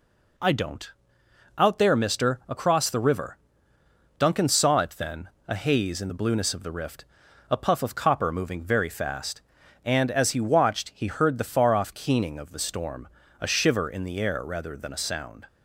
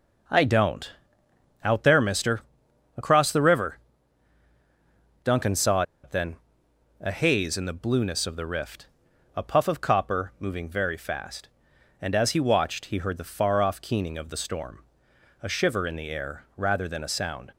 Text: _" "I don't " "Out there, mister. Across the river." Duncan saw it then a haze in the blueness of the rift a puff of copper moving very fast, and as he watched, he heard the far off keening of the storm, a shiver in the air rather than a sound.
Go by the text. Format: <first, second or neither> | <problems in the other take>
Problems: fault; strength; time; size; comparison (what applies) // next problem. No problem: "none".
first | pauses between "saw" and "it"; slight; at 5.8 s; 0.20 s long // pauses between "then" and "a"; noticeable; at 6.3 s; 0.66 s long; slight in the first // pauses between "rift" and "a"; noticeable; at 8.8 s; 0.50 s long; also in the first